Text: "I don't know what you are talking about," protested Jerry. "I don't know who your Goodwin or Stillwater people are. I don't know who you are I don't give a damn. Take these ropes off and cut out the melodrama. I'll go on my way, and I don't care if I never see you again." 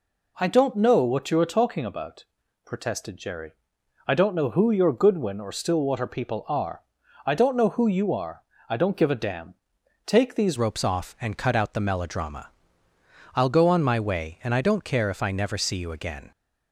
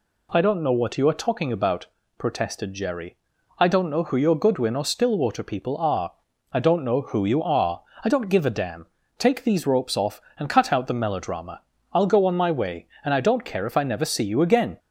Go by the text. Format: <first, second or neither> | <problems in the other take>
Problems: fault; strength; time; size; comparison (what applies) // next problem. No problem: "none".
second | pauses between "are" and "I"; slight; at 8.4 s; 0.26 s long; slight in the second // changes voice at "ropes"; from 10.5 s on; 5.8 s long